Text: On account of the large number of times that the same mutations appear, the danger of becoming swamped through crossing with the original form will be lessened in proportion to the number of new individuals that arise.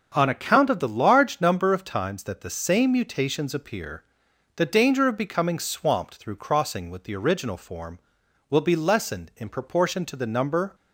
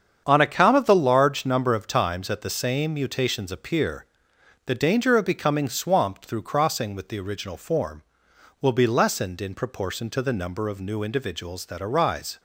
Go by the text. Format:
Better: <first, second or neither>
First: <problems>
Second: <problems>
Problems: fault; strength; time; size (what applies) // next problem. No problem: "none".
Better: second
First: starts louder than the rest; until 1.1 s; 6.5 dB // stops before "of new individuals that arise"; at 10.7 s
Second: starts louder than the rest; strong; until 1.2 s; 8 dB